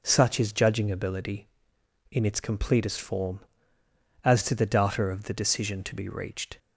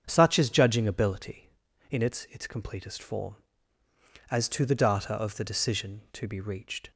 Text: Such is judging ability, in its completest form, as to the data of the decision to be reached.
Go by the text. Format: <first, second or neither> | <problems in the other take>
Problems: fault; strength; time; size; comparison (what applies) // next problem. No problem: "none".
first | starts louder than the rest; strong; until 1.0 s; 7.5 dB // says "its" twice; at 2.3 s